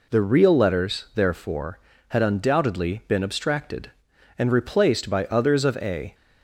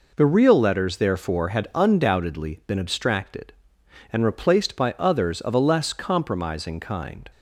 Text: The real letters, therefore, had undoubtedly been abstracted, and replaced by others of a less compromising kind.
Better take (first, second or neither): second